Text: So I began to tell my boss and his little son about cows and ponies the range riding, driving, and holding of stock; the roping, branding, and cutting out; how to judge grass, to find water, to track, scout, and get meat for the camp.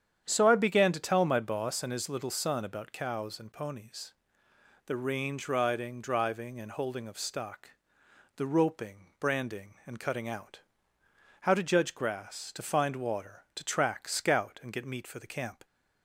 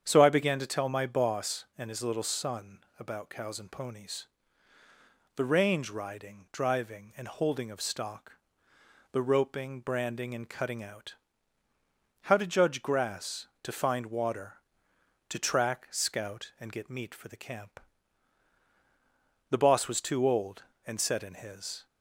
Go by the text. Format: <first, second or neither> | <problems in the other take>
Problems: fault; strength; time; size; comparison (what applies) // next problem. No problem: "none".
first | starts louder than the rest; strong; until 1.0 s; 8 dB; strong in the first // pauses between "son" and "about"; slight; at 2.7 s; 0.20 s long // pauses between "ponies" and "the"; at 4.2 s; 1.1 s long; noticeable in the first // goes on to say "The boss was too old and set in his"; strong; from 19.4 s on; 2.3 s long